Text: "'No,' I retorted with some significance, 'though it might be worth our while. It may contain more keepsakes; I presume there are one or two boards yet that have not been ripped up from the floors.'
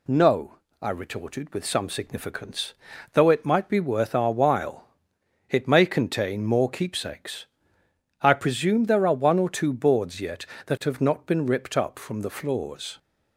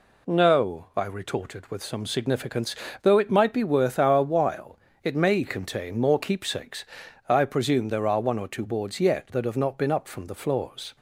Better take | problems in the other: first | skips "ripped"; at 9.9 s

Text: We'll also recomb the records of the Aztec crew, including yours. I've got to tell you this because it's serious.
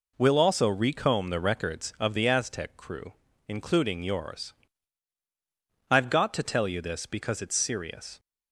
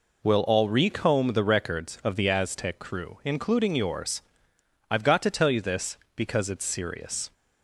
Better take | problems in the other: first | says "all" for "also"; at 0.4 s

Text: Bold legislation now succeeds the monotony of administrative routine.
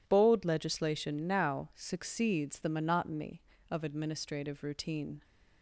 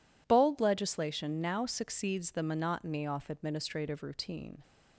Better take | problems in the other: first | says "off" for "of"; at 3.0 s

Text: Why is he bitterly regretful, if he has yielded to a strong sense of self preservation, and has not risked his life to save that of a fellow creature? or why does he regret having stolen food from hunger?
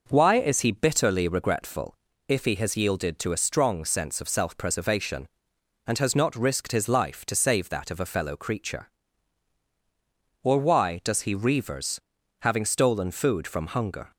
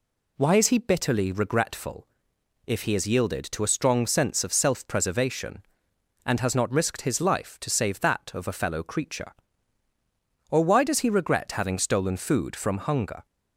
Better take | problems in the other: second | says "reavers" for "regret"; at 11.3 s

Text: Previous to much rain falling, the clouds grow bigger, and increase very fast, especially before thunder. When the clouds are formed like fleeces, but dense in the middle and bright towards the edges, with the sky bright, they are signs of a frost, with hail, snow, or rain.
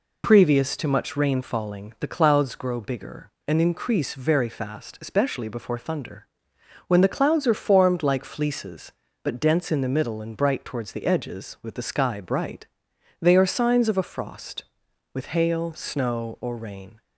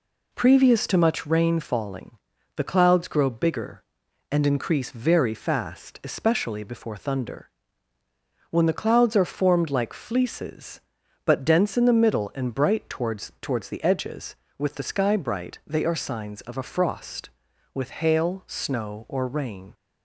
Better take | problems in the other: first | says "towards" twice; at 13.3 s

